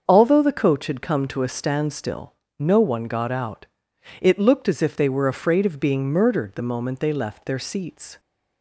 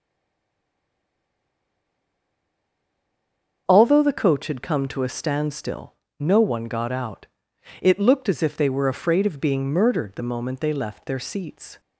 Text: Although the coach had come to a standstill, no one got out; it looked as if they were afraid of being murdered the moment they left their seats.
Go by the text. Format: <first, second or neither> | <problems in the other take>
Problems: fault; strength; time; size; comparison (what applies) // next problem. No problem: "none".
first | stays silent before the first word; strong; until 3.6 s; 3.6 s long // starts louder than the rest; until 4.6 s; 6.5 dB; also in the first